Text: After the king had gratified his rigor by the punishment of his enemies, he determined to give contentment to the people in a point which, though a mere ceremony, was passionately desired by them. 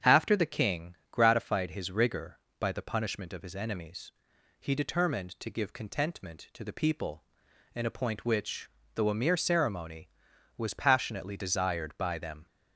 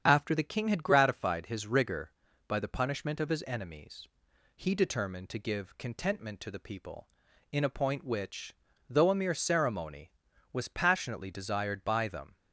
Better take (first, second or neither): second